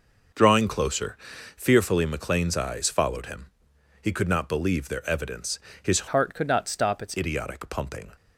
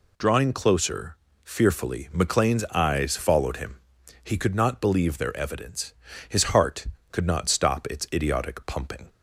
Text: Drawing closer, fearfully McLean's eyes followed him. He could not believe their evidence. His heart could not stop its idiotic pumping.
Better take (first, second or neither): second